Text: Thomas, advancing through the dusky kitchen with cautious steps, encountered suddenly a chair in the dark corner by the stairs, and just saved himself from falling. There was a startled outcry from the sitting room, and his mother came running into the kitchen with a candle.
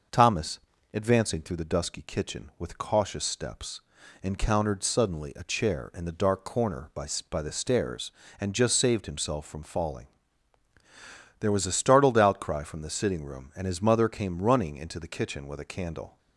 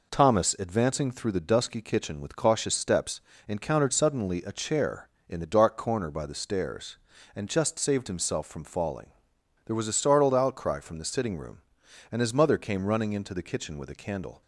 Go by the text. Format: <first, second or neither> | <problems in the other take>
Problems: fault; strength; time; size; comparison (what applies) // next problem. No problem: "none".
second | starts louder than the rest; noticeable; until 1.4 s; 6 dB // says "by" twice; at 7.2 s